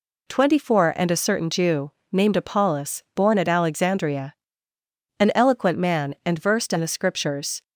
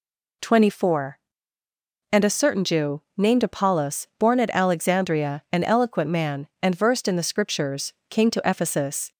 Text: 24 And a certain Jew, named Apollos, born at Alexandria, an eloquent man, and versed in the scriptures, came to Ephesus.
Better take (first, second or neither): second